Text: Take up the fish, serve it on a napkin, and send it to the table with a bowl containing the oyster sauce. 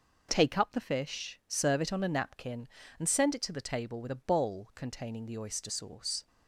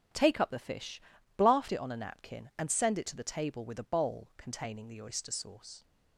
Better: first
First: none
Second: starts louder than the rest; strong; until 1.5 s; 10 dB // says "blaft" for "serve"; at 1.3 s

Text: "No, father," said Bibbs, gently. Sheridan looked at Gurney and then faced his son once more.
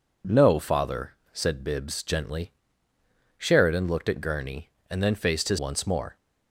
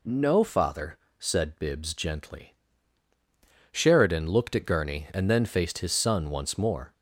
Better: second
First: skips "son"; at 5.5 s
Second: none

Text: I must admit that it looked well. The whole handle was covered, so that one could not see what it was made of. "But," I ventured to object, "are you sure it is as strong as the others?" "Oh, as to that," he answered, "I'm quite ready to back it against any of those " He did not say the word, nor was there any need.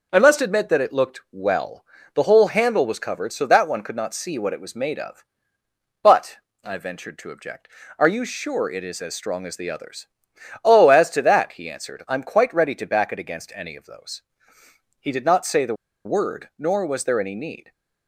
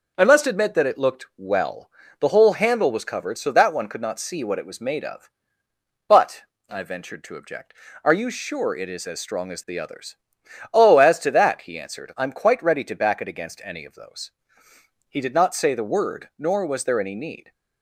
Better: second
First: pauses between "the" and "word"; slight; at 15.7 s; 0.31 s long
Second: none

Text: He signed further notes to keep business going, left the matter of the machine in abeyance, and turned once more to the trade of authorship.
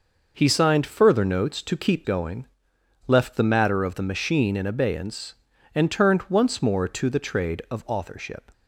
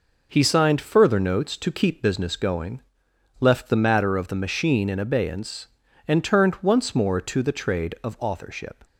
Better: second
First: skips "business"; at 2.0 s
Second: none

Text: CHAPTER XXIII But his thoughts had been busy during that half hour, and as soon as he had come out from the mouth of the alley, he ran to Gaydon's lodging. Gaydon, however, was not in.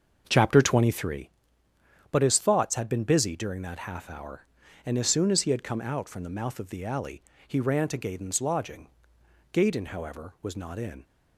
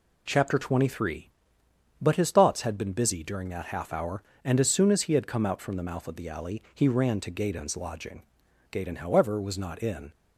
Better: second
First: starts louder than the rest; until 1.3 s; 6.5 dB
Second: none

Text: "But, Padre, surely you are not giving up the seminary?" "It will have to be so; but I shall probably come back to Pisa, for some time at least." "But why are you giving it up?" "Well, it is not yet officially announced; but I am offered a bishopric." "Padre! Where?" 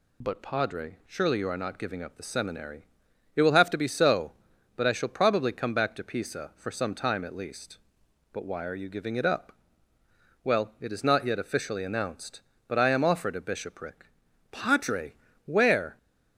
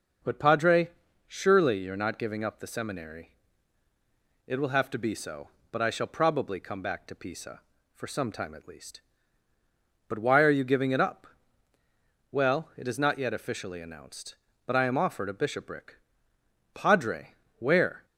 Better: neither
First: none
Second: none

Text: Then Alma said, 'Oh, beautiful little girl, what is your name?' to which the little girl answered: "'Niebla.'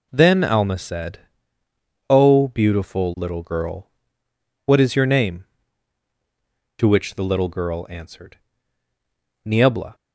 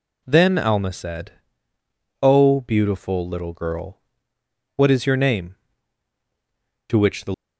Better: first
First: none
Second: stops before "little girl answered Niebla"; at 7.3 s

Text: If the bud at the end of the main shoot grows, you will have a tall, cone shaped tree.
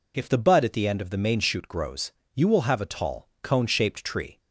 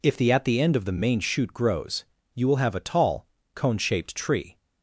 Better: first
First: none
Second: skips "bud"; at 0.3 s

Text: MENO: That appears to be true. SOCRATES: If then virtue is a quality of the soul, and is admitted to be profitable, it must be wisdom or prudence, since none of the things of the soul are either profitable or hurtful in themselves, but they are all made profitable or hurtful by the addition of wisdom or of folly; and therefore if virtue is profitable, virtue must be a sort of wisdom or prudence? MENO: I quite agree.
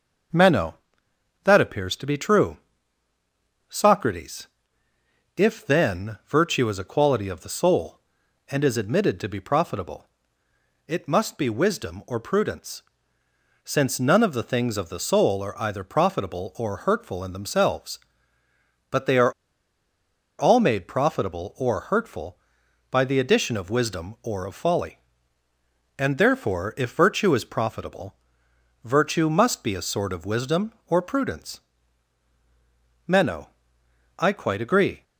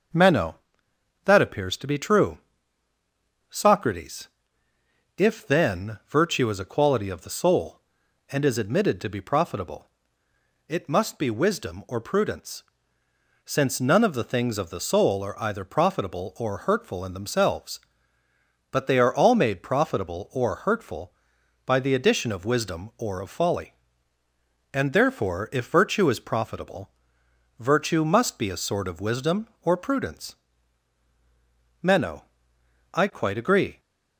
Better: second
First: starts louder than the rest; noticeable; until 2.0 s; 6 dB // pauses between "are" and "all"; at 19.3 s; 1.0 s long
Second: starts louder than the rest; noticeable; until 1.8 s; 6 dB

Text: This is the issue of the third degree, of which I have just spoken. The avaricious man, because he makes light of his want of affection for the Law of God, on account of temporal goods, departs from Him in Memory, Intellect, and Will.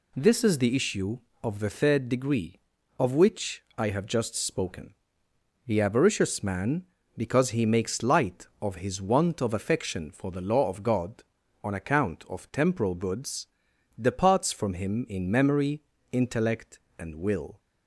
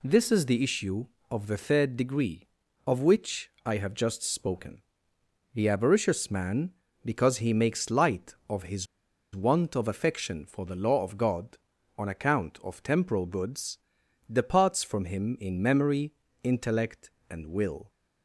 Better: first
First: pauses between "which" and "I"; slight; at 3.6 s; 0.16 s long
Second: pauses between "which" and "I"; slight; at 3.4 s; 0.16 s long // pauses between "his" and "want"; noticeable; at 8.8 s; 0.49 s long

